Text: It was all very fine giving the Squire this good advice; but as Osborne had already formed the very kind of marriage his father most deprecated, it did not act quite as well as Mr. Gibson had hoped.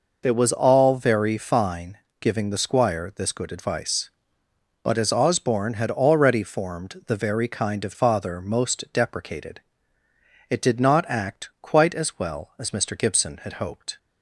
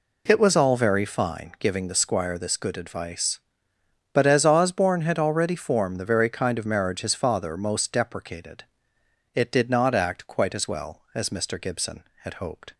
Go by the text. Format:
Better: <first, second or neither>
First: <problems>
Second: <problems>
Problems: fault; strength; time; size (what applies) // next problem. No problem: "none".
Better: second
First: pauses between "fine" and "giving"; slight; at 1.9 s; 0.22 s long // skips "marriage his"; at 7.9 s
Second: none